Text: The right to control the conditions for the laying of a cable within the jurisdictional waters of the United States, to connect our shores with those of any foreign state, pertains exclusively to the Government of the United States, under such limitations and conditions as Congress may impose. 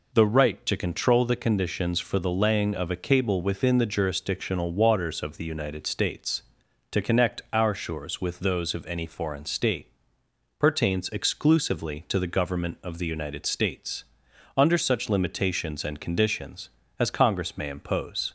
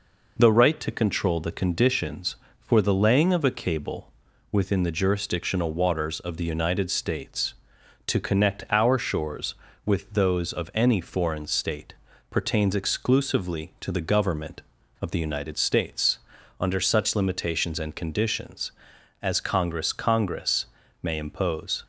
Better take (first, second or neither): first